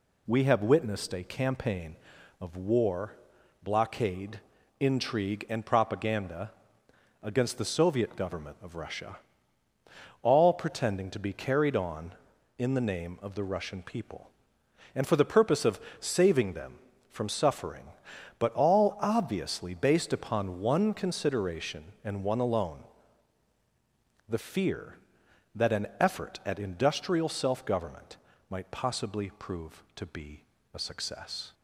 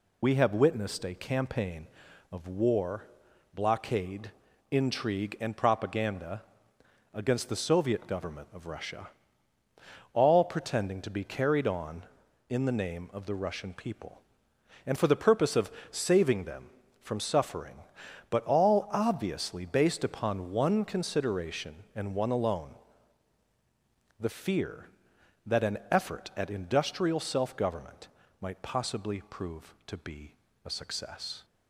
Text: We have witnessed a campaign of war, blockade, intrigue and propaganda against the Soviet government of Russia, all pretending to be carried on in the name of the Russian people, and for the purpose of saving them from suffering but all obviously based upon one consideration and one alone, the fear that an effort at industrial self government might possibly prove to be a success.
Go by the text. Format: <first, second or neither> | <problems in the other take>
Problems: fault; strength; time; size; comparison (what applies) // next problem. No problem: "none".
first | loses the start of "We"; at 0.2 s; 40 ms // pauses between "propaganda" and "against"; noticeable; at 6.4 s; 0.72 s long; noticeable in the first // pauses between "of" and "saving"; slight; at 15.7 s; 0.20 s long; slight in the first // pauses between "government" and "might"; slight; at 28.0 s; 0.32 s long; slight in the first // pauses between "be" and "a"; slight; at 30.3 s; 0.30 s long; slight in the first